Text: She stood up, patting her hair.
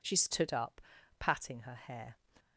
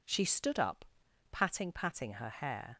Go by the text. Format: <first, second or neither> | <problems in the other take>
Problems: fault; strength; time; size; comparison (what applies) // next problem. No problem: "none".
first | says "patting" twice; at 1.7 s